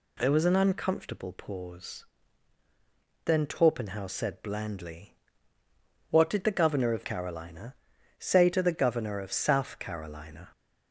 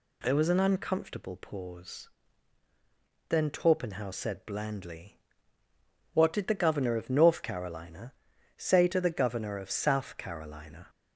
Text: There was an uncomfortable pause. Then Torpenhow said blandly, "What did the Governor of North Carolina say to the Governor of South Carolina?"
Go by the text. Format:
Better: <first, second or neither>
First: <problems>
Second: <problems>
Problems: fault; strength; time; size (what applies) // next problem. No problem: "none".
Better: second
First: skips "North"; at 7.0 s // pauses between "Carolina" and "say"; at 7.7 s; 0.42 s long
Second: pauses between "Carolina" and "say"; at 8.1 s; 0.42 s long